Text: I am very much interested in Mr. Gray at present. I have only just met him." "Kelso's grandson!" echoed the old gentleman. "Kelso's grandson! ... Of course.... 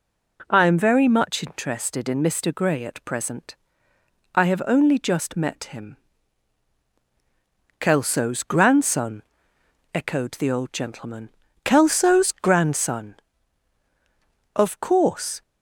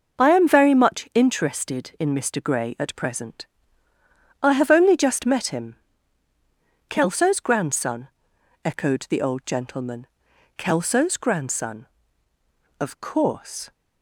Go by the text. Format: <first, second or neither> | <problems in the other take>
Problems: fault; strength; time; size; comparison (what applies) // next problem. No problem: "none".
neither | none